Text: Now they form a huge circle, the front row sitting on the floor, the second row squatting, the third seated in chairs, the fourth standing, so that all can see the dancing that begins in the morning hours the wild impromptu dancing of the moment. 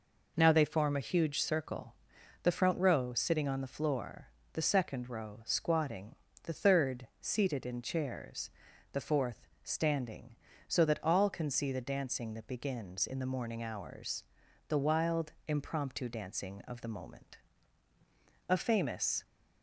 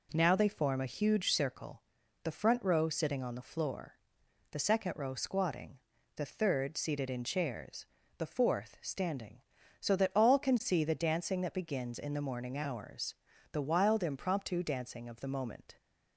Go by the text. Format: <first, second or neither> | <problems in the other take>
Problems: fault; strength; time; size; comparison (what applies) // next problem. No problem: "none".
second | pauses between "fourth" and "standing"; slight; at 9.4 s; 0.18 s long // pauses between "hours" and "the"; noticeable; at 14.2 s; 0.46 s long; also in the second // pauses between "wild" and "impromptu"; slight; at 15.3 s; 0.16 s long // goes on to say "A famous"; noticeable; from 18.4 s on; 0.78 s long